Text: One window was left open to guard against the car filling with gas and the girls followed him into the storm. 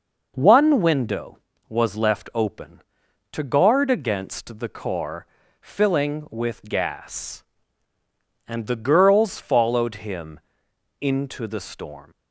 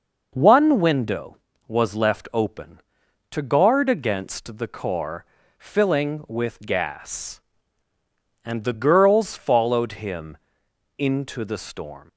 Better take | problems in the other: neither | pauses between "car" and "filling"; slight; the same in both // pauses between "him" and "into"; noticeable; the same in both

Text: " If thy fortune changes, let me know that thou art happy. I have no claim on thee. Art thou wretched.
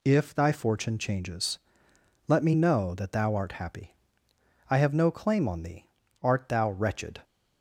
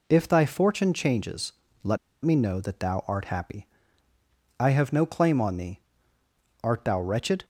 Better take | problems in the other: first | pauses between "let" and "me"; slight; at 1.9 s; 0.24 s long

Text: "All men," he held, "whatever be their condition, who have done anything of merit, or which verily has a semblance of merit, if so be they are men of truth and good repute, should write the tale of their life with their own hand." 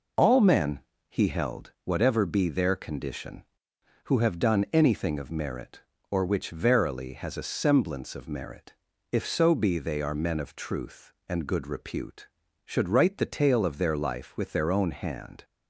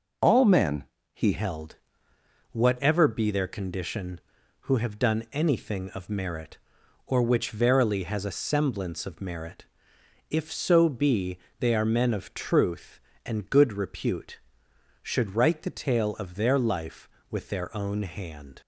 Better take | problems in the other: first | changes voice at "held"; from 1.3 s on; 17.3 s long // pauses between "be" and "they"; slight; at 11.3 s; 0.20 s long

